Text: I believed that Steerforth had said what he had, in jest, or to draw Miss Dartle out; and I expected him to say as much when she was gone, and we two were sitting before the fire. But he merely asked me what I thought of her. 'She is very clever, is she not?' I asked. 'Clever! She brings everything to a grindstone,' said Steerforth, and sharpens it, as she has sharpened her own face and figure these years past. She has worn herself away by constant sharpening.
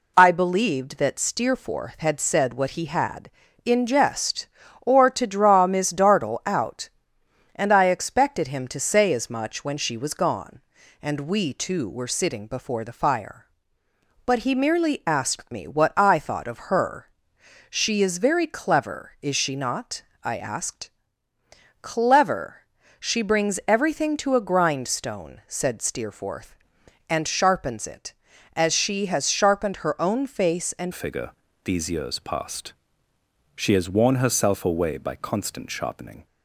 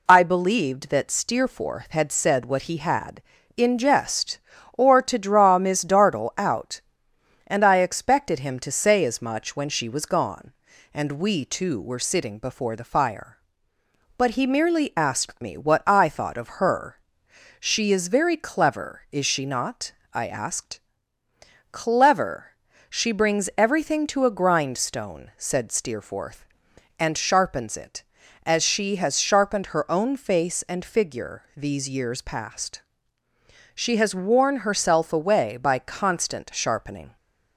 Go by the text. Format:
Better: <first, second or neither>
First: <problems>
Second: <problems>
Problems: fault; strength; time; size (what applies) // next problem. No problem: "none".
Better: second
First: changes voice at "figure"; from 30.9 s on; 5.3 s long // pauses between "figure" and "these"; slight; at 31.3 s; 0.32 s long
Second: none